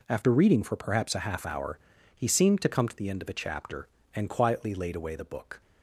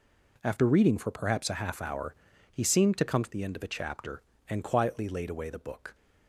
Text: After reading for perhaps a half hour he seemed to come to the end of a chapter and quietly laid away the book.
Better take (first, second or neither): neither